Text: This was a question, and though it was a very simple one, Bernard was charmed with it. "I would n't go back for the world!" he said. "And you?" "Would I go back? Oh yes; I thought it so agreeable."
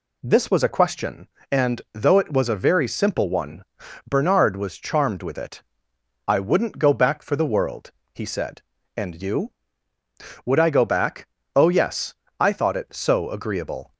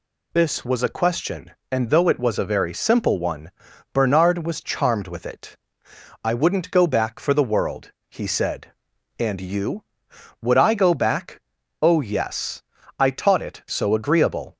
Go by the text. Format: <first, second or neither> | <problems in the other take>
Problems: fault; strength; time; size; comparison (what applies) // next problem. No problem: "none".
first | says "taught" for "thought"; at 13.0 s